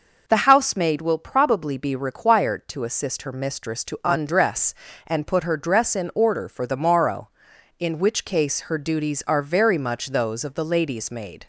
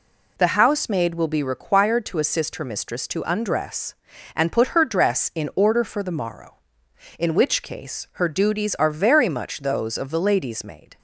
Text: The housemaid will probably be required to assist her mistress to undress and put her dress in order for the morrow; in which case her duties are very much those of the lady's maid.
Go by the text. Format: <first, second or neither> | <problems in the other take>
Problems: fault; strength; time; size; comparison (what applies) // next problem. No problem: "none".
first | skips "probably"; at 1.2 s